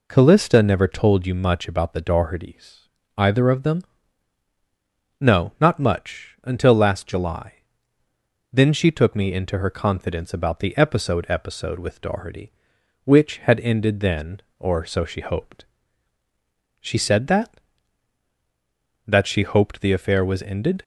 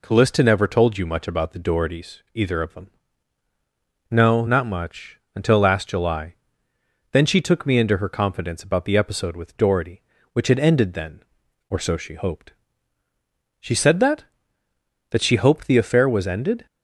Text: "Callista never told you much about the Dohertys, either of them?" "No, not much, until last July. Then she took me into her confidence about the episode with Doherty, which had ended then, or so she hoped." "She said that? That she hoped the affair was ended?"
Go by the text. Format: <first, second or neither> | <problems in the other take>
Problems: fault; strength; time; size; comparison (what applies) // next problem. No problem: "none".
second | says "episode" twice; at 11.2 s